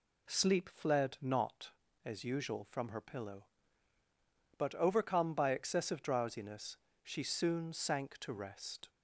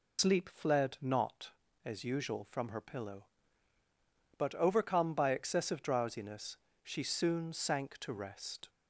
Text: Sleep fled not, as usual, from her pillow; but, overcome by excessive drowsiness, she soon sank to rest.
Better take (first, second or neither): first